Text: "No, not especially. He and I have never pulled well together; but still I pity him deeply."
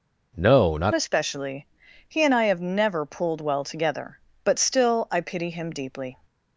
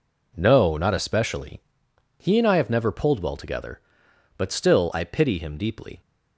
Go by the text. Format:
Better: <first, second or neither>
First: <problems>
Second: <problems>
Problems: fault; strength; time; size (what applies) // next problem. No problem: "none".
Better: second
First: changes voice at "especially"; from 0.9 s on; 5.2 s long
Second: none